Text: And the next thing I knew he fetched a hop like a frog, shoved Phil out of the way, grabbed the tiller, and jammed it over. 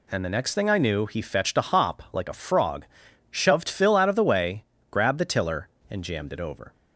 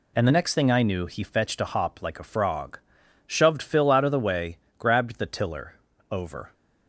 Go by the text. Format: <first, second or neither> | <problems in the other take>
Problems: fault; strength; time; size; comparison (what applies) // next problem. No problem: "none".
first | skips "and jammed it"; at 5.9 s